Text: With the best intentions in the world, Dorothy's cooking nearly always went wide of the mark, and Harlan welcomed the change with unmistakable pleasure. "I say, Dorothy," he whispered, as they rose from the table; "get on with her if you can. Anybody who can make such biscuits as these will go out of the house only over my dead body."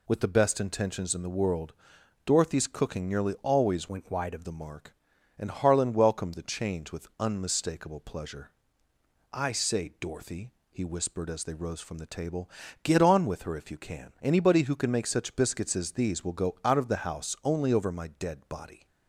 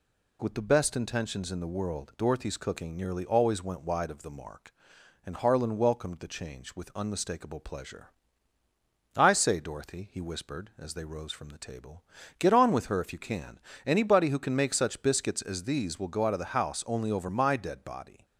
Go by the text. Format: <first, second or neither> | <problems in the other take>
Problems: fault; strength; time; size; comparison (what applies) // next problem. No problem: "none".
second | changes voice from "went" to "of"; from 3.8 to 4.4 s; 0.6 s long